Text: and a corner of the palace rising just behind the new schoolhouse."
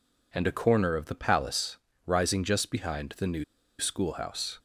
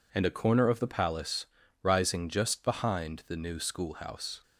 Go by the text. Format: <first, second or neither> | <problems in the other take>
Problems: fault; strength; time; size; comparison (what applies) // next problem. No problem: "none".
second | pauses between "palace" and "rising"; slight; at 1.7 s; 0.30 s long; slight in the second // pauses between "new" and "schoolhouse"; slight; at 3.4 s; 0.34 s long